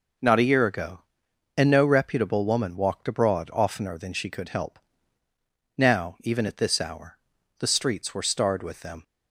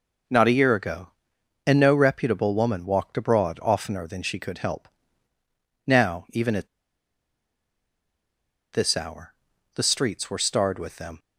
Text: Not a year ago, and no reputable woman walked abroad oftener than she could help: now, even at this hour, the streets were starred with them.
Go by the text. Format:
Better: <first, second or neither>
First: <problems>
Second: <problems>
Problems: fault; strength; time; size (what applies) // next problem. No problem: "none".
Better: first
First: none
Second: pauses between "at" and "this"; strong; at 6.6 s; 2.0 s long